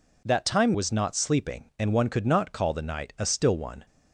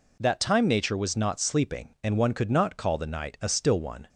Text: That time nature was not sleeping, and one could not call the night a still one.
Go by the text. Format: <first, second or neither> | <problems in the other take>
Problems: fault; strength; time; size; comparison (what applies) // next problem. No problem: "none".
second | skips "nature"; at 0.7 s